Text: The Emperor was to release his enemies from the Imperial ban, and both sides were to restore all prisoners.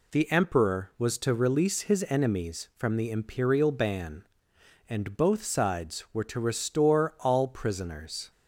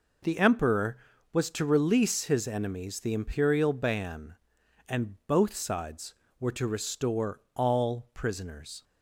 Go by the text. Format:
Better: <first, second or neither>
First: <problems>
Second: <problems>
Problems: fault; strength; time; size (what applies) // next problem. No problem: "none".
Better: first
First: none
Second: skips "from"; at 2.9 s